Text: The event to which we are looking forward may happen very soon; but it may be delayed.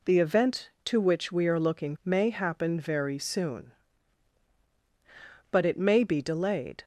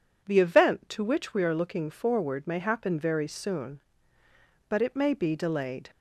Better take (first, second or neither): second